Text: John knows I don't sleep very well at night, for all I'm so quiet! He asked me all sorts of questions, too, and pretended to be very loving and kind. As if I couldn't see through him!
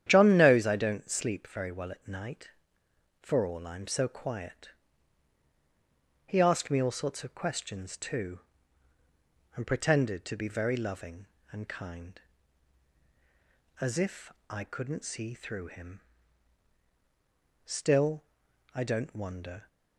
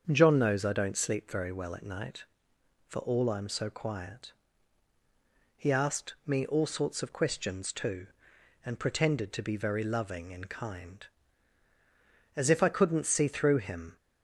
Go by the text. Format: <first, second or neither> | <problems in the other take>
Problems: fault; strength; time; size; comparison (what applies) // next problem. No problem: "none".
second | starts louder than the rest; strong; until 1.0 s; 10 dB; also in the second // pauses between "if" and "I"; slight; at 14.3 s; 0.18 s long // goes on to say "Still I don't wonder"; strong; from 17.6 s on; 2.0 s long